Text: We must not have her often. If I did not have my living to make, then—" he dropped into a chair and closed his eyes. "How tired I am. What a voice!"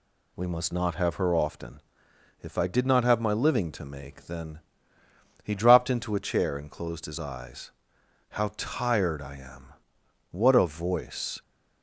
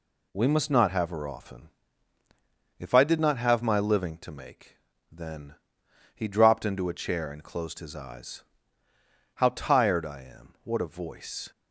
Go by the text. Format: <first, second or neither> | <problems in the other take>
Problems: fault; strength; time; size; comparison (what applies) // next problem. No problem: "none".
neither | none